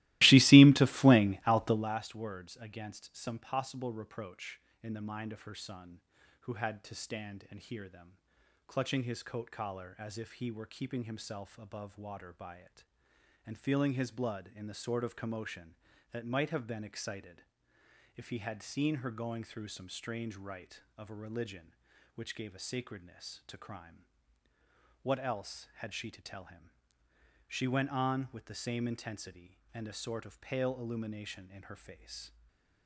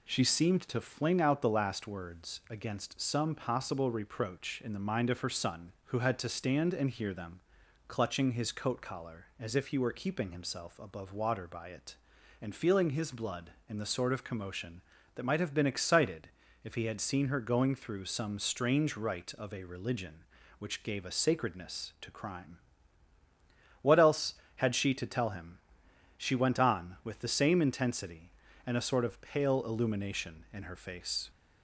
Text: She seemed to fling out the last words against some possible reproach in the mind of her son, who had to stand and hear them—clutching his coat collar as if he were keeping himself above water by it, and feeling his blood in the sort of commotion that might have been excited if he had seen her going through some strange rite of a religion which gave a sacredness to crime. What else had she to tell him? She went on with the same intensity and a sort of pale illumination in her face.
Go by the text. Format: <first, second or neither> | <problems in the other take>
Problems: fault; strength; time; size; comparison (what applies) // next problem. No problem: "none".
second | starts louder than the rest; strong; until 2.0 s; 18 dB // pauses between "excited" and "if"; noticeable; at 17.4 s; 0.72 s long; slight in the second // stays silent after the last word; slight; from 32.2 s on; 0.6 s long